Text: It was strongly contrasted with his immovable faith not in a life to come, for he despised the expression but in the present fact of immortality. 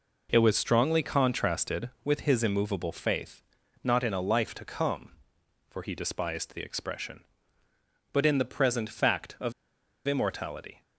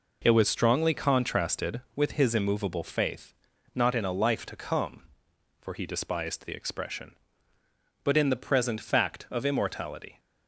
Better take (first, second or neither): second